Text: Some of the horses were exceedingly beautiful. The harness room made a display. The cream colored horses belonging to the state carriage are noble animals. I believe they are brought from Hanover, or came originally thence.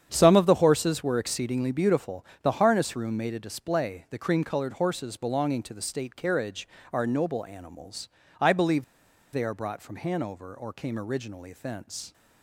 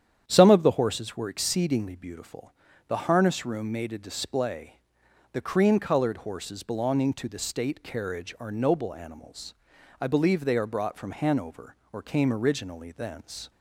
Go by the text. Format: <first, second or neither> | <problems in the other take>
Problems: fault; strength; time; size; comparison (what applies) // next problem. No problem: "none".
second | starts louder than the rest; strong; until 1.1 s; 8.5 dB; strong in the second // pauses between "believe" and "they"; noticeable; at 8.8 s; 0.50 s long